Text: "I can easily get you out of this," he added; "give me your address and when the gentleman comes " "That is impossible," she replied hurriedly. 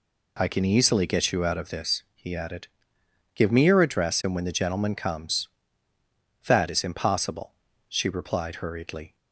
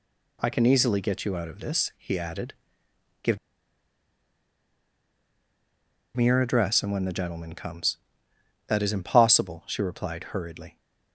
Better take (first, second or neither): first